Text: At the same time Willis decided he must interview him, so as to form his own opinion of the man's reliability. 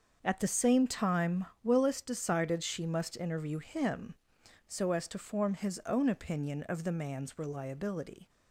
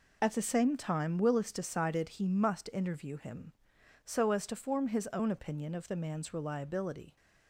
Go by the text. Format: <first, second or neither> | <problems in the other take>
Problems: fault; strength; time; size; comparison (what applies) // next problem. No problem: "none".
second | starts louder than the rest; until 1.2 s; 6.5 dB // pauses between "time" and "Willis"; slight; at 1.4 s; 0.18 s long // says "she" for "he"; at 2.6 s